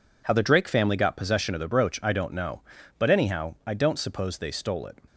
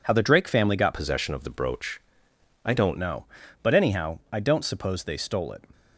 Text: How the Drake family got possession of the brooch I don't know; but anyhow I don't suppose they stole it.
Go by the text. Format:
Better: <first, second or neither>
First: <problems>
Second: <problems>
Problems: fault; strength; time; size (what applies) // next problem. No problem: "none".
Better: first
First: none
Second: changes voice from "possession" to "don't"; from 0.9 to 2.9 s; 2.0 s long // pauses between "brooch" and "I"; noticeable; at 1.9 s; 0.64 s long